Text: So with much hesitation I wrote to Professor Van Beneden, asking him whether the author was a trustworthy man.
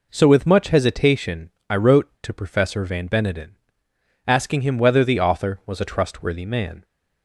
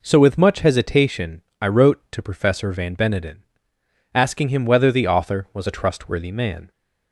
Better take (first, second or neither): neither